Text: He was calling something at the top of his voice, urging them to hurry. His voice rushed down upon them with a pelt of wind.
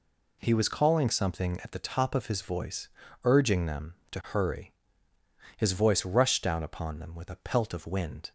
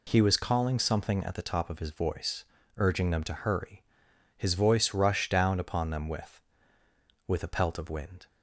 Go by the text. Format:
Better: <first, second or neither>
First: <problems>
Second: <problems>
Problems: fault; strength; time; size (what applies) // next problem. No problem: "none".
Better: first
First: none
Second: says "with" twice; at 7.2 s